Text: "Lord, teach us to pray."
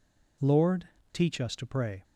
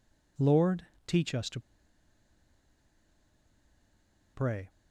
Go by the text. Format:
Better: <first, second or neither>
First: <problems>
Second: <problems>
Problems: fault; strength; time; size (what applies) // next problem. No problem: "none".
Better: first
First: none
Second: pauses between "to" and "pray"; strong; at 1.5 s; 2.7 s long